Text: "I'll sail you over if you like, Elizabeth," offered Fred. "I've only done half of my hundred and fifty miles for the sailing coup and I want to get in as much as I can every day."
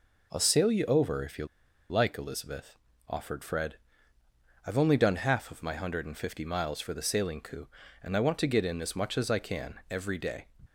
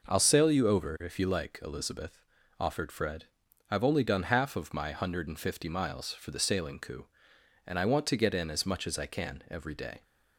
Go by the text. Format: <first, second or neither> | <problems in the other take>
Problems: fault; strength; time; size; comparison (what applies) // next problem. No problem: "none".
second | pauses between "you" and "like"; at 1.4 s; 0.44 s long